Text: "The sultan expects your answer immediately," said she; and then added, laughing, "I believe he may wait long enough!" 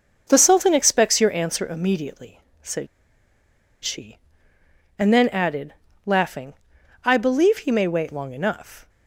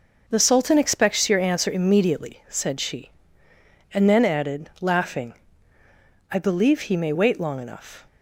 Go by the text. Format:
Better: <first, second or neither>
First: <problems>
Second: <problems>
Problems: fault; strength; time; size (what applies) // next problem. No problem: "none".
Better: second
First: starts louder than the rest; until 1.2 s; 6.5 dB // pauses between "said" and "she"; noticeable; at 2.8 s; 0.97 s long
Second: none